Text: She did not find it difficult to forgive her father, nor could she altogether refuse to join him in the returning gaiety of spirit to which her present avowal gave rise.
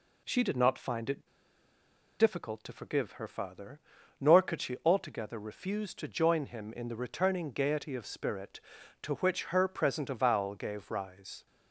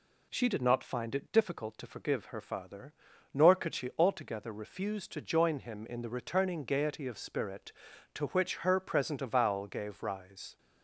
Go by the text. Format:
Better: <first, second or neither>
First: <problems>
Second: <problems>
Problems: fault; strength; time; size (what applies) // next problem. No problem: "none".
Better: second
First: pauses between "it" and "difficult"; noticeable; at 1.2 s; 0.93 s long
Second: none